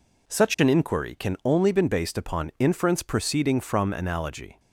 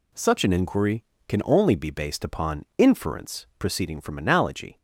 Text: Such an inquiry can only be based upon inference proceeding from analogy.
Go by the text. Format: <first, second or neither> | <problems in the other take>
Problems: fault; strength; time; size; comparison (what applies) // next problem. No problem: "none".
second | says "been" for "be"; at 1.7 s